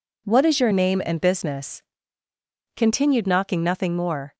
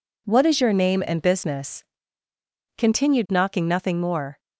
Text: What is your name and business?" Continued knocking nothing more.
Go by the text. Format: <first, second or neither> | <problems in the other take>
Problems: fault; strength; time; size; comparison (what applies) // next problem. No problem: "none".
neither | none